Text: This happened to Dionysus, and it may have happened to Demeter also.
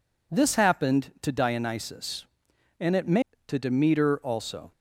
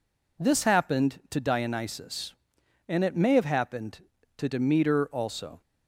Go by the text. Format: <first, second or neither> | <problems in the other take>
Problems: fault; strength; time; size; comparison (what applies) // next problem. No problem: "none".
second | skips "have happened"; at 3.3 s